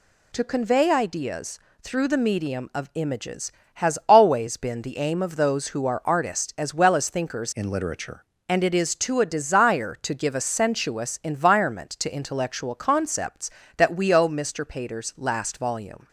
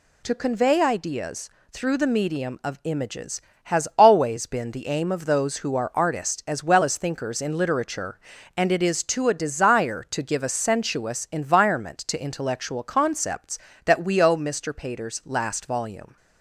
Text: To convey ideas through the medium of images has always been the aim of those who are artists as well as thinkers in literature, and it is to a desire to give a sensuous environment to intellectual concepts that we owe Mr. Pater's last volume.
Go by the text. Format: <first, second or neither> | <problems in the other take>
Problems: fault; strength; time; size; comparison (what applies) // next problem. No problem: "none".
second | pauses between "ideas" and "through"; slight; at 1.5 s; 0.24 s long; slight in the second // changes voice from "in" to "literature"; from 7.5 to 8.2 s; 0.7 s long